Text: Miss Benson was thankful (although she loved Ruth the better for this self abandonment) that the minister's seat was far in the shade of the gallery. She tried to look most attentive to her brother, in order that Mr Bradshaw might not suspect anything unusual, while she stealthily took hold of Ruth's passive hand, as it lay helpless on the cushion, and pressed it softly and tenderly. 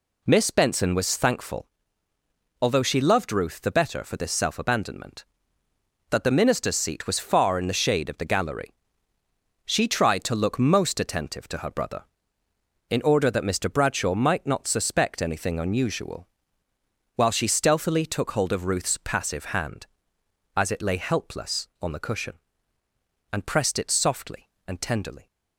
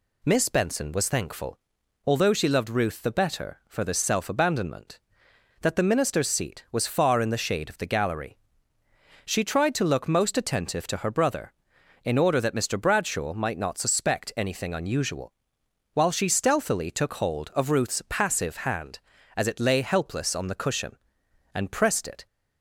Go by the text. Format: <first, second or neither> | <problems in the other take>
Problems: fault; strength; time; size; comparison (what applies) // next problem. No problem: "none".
first | stops before "softly and tenderly"; at 22.2 s